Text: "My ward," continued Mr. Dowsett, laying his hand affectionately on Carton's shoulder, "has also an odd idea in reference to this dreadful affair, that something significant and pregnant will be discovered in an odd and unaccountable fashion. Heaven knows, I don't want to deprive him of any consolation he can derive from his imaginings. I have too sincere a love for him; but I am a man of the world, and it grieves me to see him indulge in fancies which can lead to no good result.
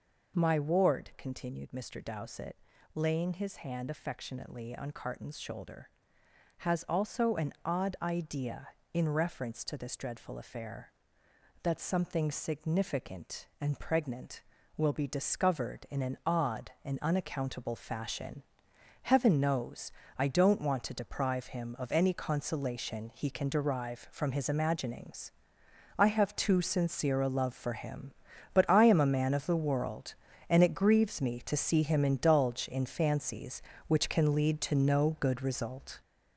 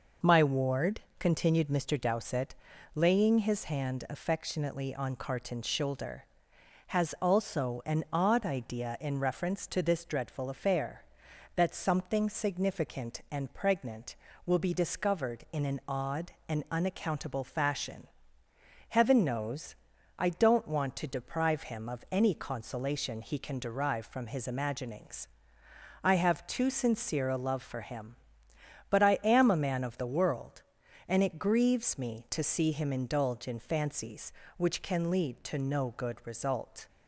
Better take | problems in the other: second | gets louder; noticeable; throughout; 6 dB

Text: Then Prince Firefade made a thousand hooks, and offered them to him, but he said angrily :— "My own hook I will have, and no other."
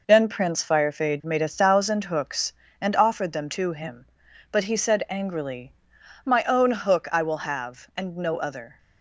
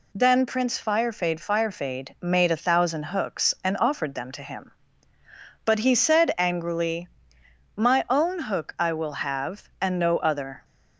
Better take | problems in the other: first | says "Firefade" twice; at 1.3 s

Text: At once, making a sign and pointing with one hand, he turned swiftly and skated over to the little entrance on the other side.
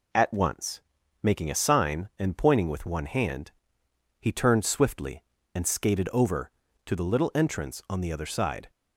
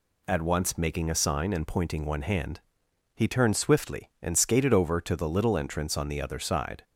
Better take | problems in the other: first | skips "with"; at 2.0 s

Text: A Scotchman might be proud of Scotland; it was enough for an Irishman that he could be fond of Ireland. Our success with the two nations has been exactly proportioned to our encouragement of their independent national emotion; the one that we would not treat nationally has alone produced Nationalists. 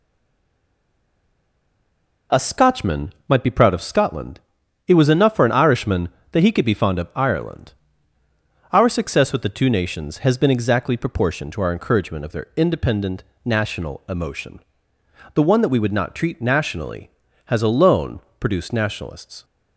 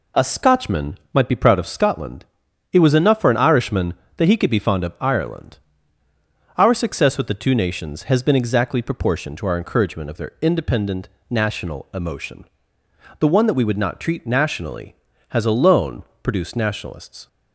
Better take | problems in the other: second | stays silent before the first word; until 2.2 s; 2.2 s long // pauses between "independent" and "national"; slight; at 13.2 s; 0.20 s long; slight in the second // pauses between "alone" and "produced"; slight; at 18.2 s; 0.18 s long; slight in the second

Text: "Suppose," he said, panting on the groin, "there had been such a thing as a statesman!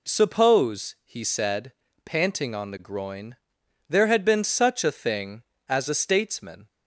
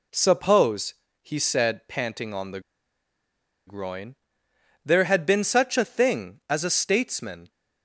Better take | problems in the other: first | pauses between "the" and "groin"; at 2.5 s; 1.0 s long

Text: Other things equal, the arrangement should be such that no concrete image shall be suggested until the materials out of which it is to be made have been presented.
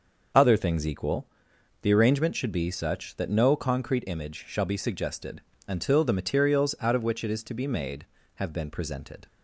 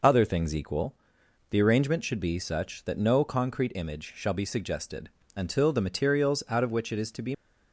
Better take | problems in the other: first | pauses between "suggested" and "until"; slight; at 5.0 s; 0.26 s long; slight in the first // stops before "made have been presented"; at 7.3 s

